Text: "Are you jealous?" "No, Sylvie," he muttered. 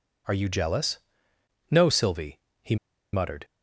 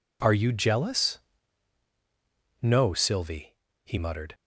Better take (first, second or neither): second